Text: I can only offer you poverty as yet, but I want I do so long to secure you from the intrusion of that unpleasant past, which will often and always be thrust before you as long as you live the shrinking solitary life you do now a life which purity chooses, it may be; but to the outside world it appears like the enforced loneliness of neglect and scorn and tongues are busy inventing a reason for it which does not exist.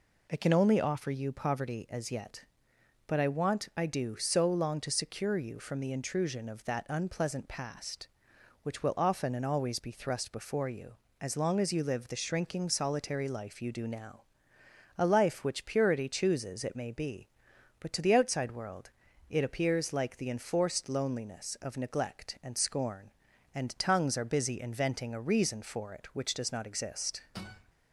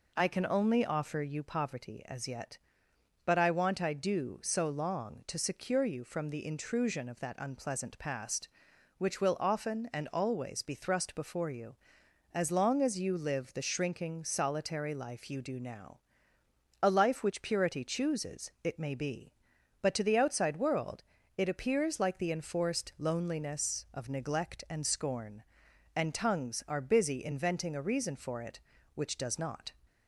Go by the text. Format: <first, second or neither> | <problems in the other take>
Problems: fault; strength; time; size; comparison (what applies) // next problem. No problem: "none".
first | pauses between "now" and "a"; noticeable; at 15.9 s; 0.84 s long; noticeable in the first // pauses between "world" and "it"; slight; at 21.0 s; 0.32 s long; also in the first // stops before "exist"; at 29.8 s